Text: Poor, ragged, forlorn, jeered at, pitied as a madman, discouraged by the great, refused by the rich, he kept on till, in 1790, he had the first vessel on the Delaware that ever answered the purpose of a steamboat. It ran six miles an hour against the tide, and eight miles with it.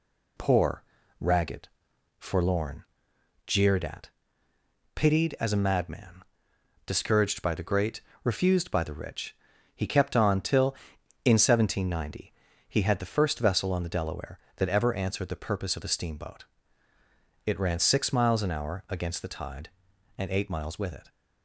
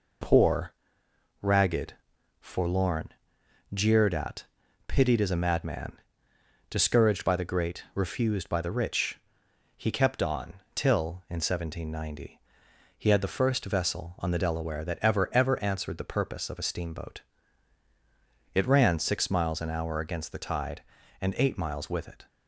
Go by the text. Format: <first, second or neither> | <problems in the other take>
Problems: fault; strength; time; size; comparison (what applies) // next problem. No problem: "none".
first | pauses between "on" and "till"; slight; at 10.5 s; 0.22 s long // says "ever" twice; at 15.3 s